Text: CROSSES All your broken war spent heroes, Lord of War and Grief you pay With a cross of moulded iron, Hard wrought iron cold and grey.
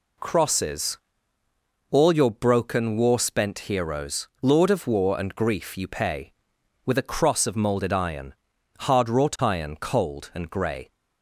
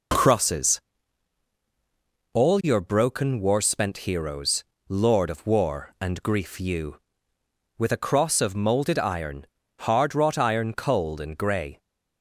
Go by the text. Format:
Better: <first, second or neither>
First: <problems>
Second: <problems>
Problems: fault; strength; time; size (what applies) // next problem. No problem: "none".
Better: first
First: pauses between "CROSSES" and "All"; noticeable; at 0.9 s; 0.94 s long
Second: pauses between "CROSSES" and "All"; strong; at 0.7 s; 1.5 s long // skips "pay"; at 7.3 s